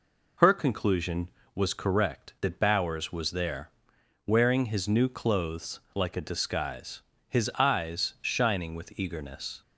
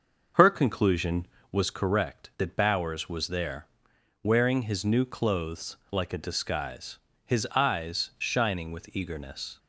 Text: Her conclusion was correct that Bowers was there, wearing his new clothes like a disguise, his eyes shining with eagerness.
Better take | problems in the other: first | starts louder than the rest; until 1.8 s; 6.5 dB

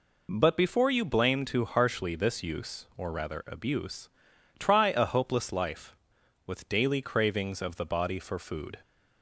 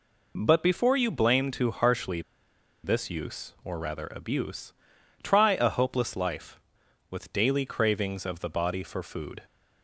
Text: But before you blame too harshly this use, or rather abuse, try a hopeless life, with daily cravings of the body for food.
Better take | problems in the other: first | pauses between "harshly" and "this"; noticeable; at 2.2 s; 0.63 s long

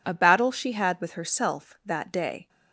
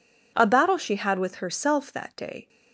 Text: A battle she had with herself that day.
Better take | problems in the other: neither | none

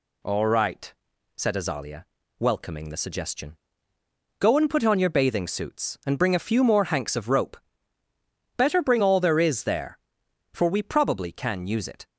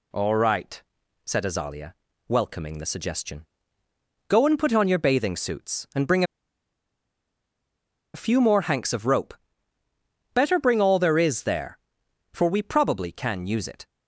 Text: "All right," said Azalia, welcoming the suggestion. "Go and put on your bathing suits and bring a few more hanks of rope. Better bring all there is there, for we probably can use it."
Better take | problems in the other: first | pauses between "bring" and "a"; strong; at 6.2 s; 1.9 s long

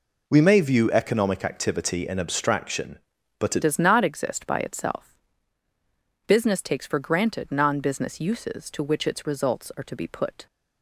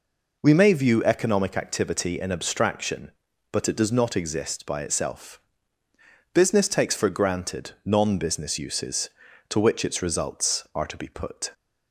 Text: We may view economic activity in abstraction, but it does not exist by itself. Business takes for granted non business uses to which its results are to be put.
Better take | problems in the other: second | changes voice at "does"; from 3.6 s on; 6.8 s long

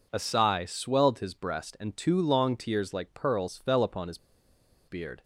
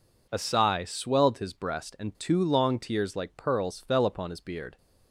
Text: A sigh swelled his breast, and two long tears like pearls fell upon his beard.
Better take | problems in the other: second | pauses between "his" and "beard"; noticeable; at 4.1 s; 0.71 s long

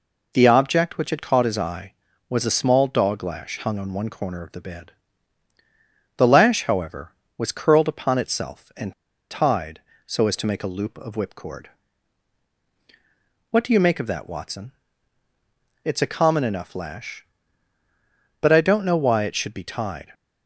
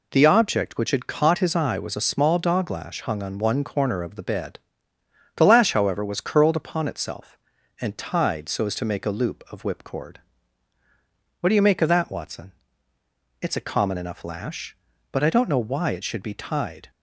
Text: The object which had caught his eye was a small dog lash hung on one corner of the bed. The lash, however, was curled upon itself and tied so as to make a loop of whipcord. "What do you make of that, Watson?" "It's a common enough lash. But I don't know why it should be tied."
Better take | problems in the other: second | pauses between "and" and "tied"; at 8.9 s; 0.38 s long

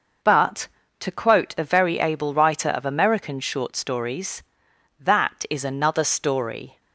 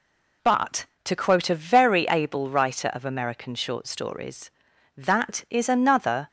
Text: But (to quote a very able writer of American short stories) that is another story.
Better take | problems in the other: first | stops before "story"; at 6.2 s

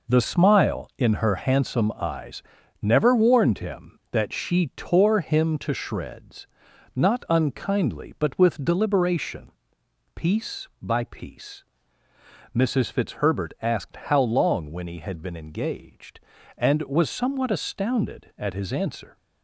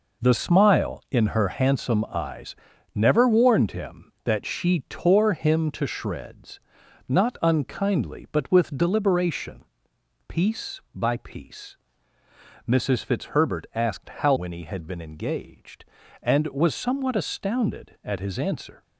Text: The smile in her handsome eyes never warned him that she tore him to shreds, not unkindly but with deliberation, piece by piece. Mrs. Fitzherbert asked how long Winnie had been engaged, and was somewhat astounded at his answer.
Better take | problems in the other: first | pauses between "eyes" and "never"; at 2.5 s; 0.40 s long; also in the first // skips "long"; at 14.3 s

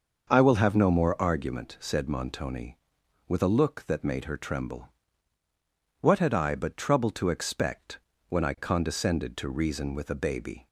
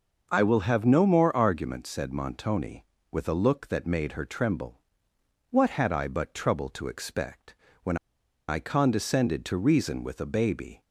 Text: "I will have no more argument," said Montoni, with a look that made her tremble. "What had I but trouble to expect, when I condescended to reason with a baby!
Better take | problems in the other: first | starts louder than the rest; noticeable; until 1.3 s; 6 dB; also in the first // pauses between "when" and "I"; noticeable; at 7.9 s; 0.52 s long

